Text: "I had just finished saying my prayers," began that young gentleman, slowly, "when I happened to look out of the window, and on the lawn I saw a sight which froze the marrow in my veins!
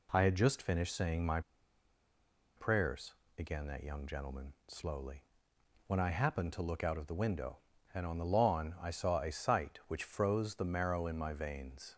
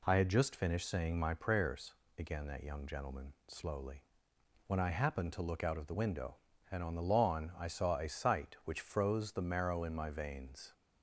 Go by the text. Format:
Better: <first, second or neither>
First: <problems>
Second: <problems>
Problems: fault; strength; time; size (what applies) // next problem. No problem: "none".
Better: second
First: pauses between "my" and "prayers"; at 1.3 s; 1.1 s long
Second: none